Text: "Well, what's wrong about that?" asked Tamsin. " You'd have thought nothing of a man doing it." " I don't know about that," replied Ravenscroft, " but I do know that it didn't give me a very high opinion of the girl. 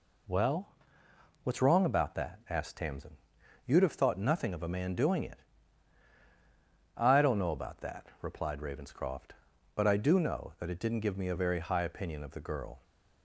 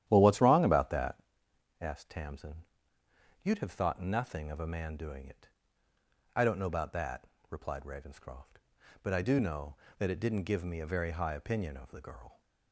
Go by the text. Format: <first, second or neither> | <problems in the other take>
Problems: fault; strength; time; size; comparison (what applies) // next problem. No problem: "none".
first | starts louder than the rest; strong; until 1.3 s; 12 dB